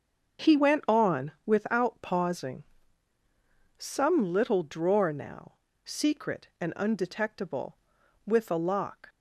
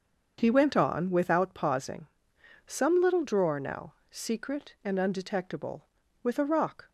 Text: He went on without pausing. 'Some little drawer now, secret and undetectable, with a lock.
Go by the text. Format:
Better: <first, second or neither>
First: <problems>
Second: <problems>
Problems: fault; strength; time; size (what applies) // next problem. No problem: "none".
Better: first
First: starts louder than the rest; until 1.5 s; 6.5 dB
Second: starts louder than the rest; until 1.4 s; 7 dB // says "rock" for "lock"; at 6.4 s